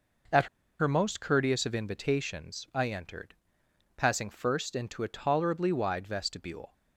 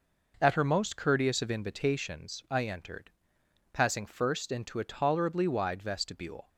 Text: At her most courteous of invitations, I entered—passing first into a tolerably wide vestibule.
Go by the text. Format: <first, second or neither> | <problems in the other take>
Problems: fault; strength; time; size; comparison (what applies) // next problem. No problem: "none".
second | pauses between "At" and "her"; slight; at 0.4 s; 0.33 s long